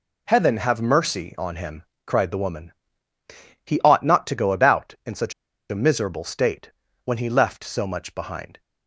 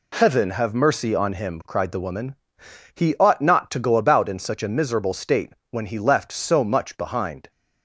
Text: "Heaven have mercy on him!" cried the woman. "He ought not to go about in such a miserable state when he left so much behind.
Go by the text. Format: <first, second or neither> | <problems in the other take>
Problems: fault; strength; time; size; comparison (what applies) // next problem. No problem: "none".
second | pauses between "such" and "a"; at 5.3 s; 0.39 s long // pauses between "state" and "when"; slight; at 6.7 s; 0.34 s long; slight in the second